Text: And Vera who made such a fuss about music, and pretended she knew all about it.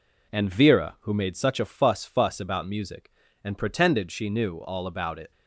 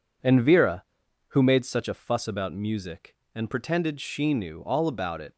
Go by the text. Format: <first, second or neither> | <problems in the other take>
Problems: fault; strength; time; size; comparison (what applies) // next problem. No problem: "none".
second | says "fuss" twice; at 2.0 s